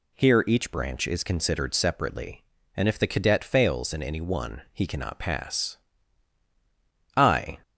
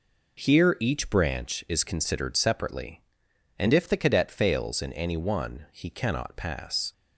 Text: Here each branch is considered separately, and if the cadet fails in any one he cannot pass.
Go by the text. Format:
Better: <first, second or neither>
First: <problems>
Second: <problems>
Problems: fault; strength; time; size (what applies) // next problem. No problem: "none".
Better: second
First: goes on to say "I"; slight; from 7.1 s on; 0.42 s long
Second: none